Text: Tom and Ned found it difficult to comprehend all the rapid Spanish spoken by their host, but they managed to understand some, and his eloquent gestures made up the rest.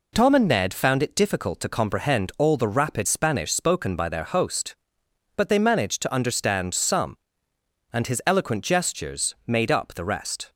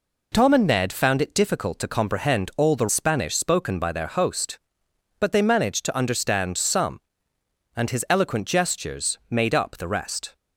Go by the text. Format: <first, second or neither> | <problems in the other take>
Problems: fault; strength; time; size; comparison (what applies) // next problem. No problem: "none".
first | skips "rapid"; at 2.8 s